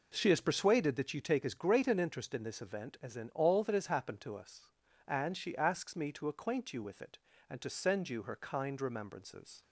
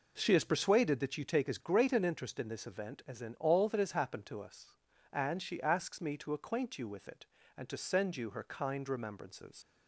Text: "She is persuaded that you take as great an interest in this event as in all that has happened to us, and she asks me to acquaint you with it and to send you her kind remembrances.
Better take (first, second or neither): first